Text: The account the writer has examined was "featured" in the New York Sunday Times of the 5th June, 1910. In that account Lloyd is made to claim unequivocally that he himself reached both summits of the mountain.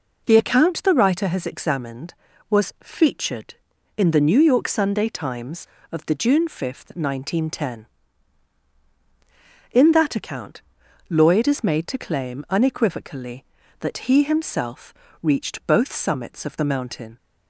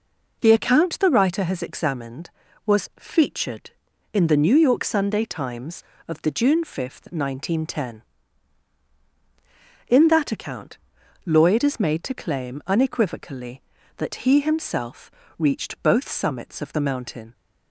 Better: neither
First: pauses between "account" and "Lloyd"; noticeable; at 10.6 s; 0.48 s long // pauses between "himself" and "reached"; slight; at 14.9 s; 0.30 s long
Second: pauses between "account" and "Lloyd"; noticeable; at 10.7 s; 0.48 s long // pauses between "himself" and "reached"; slight; at 15.1 s; 0.28 s long

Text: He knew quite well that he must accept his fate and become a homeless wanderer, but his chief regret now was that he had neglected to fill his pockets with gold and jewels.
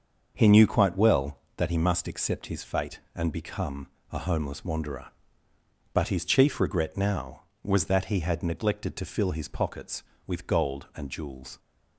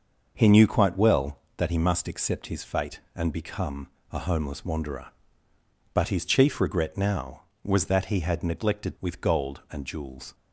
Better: first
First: starts louder than the rest; until 1.3 s; 6.5 dB // pauses between "become" and "a"; slight; at 3.8 s; 0.24 s long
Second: starts louder than the rest; noticeable; until 1.3 s; 6 dB // pauses between "become" and "a"; slight; at 3.8 s; 0.24 s long // skips "to fill his pockets"; at 8.9 s

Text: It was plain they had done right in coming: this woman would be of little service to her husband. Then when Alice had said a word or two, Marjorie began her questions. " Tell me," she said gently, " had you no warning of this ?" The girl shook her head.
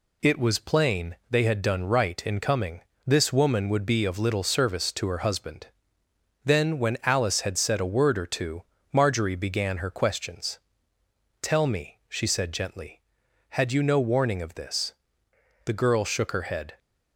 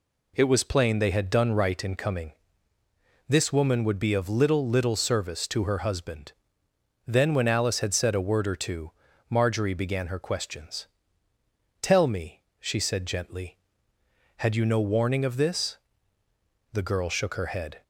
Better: first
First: none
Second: says "little" twice; at 4.6 s

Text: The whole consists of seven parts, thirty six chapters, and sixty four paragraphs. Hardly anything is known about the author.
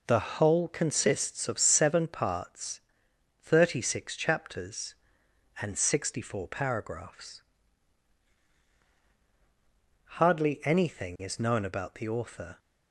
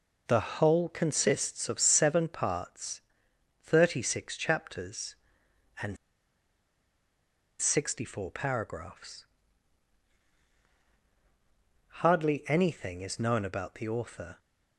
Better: first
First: none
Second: pauses between "and" and "sixty"; strong; at 5.9 s; 1.6 s long

